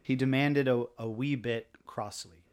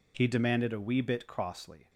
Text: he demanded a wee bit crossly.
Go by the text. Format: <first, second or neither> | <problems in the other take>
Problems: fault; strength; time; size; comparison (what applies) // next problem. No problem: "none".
second | says "a" twice; at 0.9 s // pauses between "bit" and "crossly"; slight; at 1.6 s; 0.18 s long